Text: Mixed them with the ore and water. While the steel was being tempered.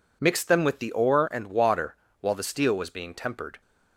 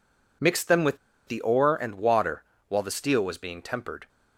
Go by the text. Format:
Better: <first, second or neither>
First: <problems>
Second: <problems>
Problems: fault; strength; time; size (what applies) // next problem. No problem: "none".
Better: first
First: none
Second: pauses between "with" and "the"; slight; at 0.9 s; 0.30 s long